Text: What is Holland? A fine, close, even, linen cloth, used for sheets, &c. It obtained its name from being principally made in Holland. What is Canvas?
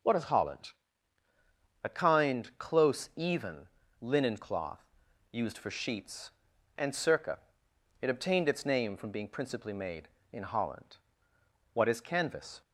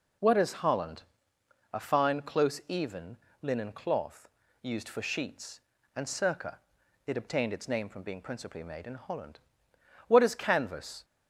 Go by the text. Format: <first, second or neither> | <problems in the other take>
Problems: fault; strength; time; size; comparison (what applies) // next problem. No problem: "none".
second | says "kind" for "fine"; at 1.8 s